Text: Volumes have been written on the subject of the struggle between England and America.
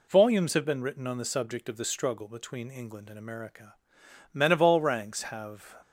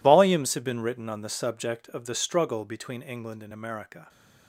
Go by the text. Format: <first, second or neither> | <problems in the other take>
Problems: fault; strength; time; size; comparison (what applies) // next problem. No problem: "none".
second | goes on to say "Men of all ranks have"; from 4.3 s on; 1.4 s long